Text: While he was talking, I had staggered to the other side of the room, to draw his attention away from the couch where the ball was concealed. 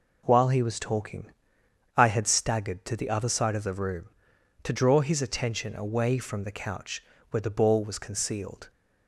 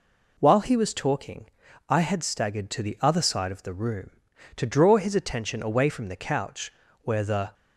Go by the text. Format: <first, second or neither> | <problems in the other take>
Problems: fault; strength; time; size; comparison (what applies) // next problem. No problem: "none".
first | pauses between "couch" and "where"; slight; at 6.7 s; 0.32 s long; slight in the first // stops before "ball was concealed"; at 7.5 s